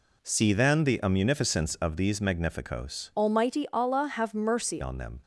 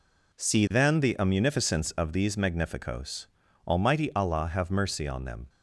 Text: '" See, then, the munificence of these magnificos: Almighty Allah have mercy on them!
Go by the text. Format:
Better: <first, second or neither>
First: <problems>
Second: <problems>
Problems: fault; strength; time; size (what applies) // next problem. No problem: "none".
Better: second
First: changes voice from "Almighty" to "mercy"; from 3.1 to 4.8 s; 1.7 s long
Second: none